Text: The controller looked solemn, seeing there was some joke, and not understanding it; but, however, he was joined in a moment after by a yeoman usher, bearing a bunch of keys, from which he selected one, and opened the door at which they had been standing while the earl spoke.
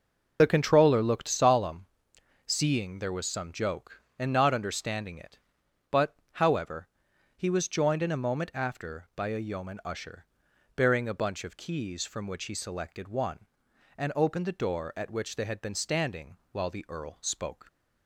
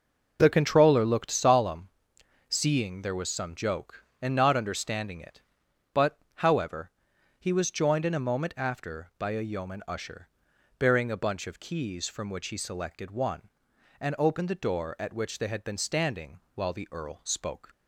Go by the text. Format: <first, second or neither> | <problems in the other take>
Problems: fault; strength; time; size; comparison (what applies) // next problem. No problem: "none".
second | loses the start of "The"; at 0.3 s; 30 ms // pauses between "standing" and "while"; slight; at 16.3 s; 0.16 s long; slight in the second